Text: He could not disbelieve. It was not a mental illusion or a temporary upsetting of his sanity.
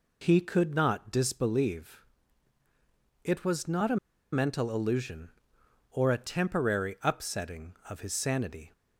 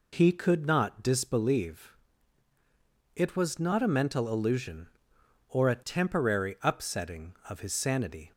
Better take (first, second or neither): second